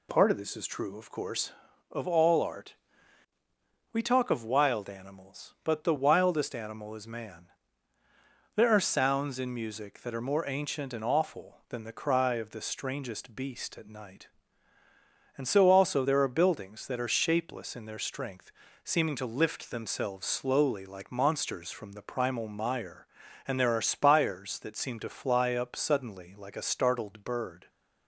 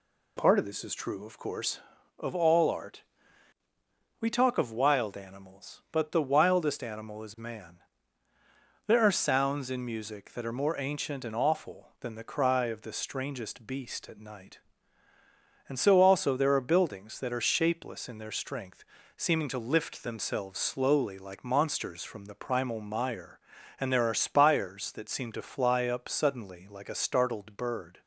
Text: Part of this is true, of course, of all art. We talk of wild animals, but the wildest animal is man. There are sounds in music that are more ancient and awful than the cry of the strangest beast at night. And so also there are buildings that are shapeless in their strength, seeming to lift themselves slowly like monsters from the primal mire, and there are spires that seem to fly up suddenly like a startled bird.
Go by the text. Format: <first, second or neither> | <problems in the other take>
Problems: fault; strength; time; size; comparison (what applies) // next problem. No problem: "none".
neither | none